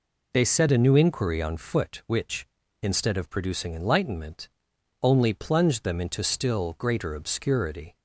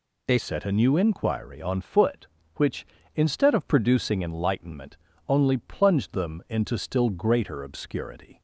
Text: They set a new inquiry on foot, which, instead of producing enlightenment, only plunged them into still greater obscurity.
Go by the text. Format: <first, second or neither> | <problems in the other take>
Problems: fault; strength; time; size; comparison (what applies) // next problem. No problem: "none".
first | changes voice at "set"; from 0.3 s on; 8.1 s long